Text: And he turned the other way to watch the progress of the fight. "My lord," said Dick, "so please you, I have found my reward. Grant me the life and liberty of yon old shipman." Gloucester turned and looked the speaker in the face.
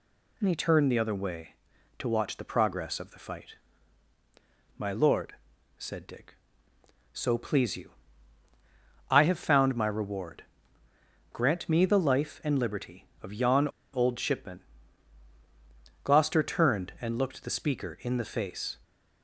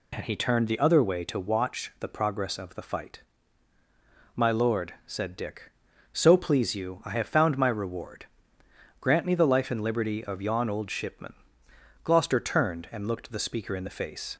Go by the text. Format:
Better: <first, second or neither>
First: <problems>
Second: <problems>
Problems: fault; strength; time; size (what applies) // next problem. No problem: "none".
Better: second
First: pauses between "yon" and "old"; slight; at 13.6 s; 0.26 s long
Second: none